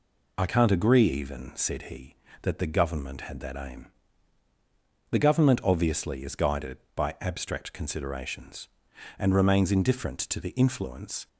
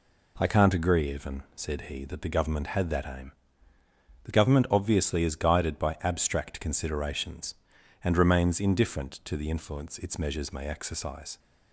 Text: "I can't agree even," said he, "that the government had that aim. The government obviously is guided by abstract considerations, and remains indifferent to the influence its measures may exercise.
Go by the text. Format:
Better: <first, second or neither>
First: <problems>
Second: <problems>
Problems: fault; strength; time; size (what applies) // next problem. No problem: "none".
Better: second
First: stops before "its measures may exercise"; at 11.2 s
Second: none